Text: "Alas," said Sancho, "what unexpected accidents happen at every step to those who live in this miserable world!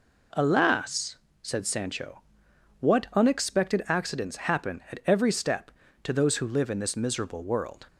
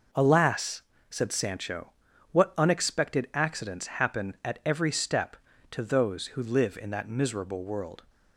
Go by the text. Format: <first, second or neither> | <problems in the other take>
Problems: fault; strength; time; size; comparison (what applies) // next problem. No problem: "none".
first | says "that" for "this"; at 6.8 s